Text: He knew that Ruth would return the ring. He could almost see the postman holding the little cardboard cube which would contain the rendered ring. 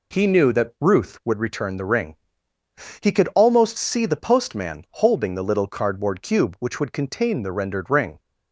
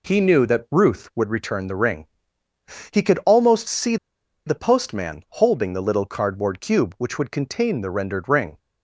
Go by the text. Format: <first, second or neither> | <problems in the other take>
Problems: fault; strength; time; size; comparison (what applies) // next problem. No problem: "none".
first | pauses between "see" and "the"; noticeable; at 3.9 s; 0.50 s long